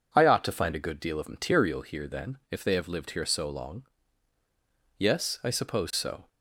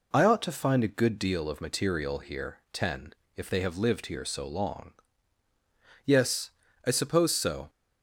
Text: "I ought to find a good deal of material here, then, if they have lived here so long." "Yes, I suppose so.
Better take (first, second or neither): first